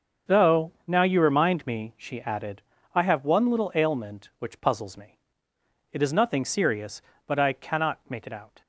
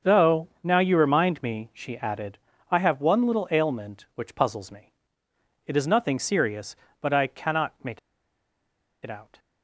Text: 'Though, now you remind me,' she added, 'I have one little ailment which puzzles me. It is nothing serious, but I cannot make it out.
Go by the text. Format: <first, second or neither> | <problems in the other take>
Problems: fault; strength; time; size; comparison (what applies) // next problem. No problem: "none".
first | starts louder than the rest; until 1.1 s; 6.5 dB; also in the first // pauses between "make" and "it"; at 7.9 s; 1.0 s long